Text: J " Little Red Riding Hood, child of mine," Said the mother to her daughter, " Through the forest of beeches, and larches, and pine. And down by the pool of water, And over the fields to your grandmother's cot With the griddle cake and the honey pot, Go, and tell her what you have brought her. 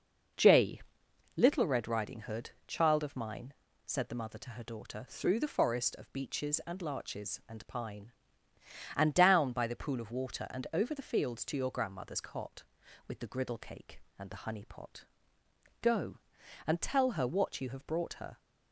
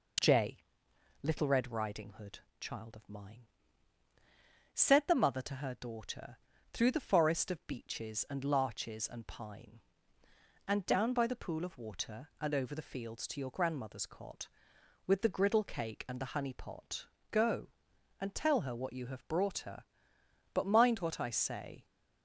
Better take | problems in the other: first | goes on to say "But mind what I say"; from 20.5 s on; 1.3 s long

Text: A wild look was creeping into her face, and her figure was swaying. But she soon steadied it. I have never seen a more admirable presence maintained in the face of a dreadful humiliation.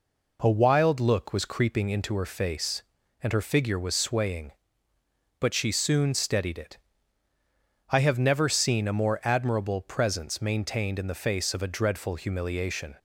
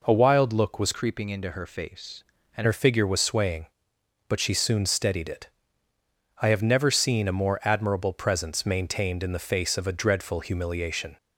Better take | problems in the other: first | changes voice from "creeping" to "and"; from 0.9 to 2.6 s; 1.7 s long

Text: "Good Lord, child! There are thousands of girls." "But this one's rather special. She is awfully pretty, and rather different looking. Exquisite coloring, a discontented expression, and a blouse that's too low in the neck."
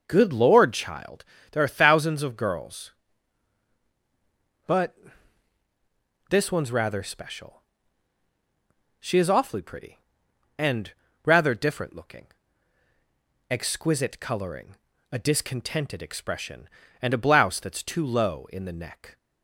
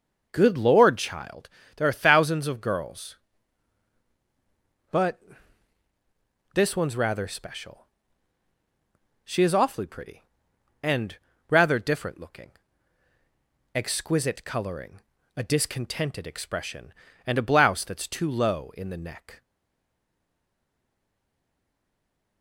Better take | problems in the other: first | starts louder than the rest; noticeable; until 1.3 s; 6 dB; noticeable in the first // pauses between "But" and "this"; strong; at 5.1 s; 1.3 s long; strong in the first // pauses between "and" and "rather"; slight; at 11.1 s; 0.32 s long; slight in the first // stays silent after the last word; strong; from 19.4 s on; 3.0 s long

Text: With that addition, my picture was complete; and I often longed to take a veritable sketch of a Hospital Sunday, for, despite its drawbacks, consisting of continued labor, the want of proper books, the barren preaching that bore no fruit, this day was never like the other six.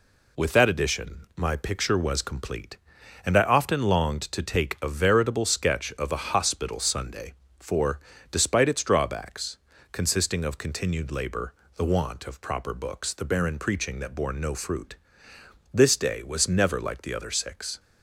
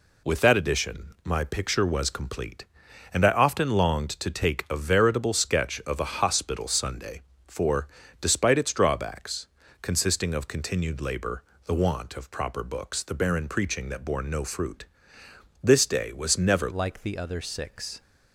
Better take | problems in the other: first | changes voice at "like"; from 16.7 s on; 1.3 s long

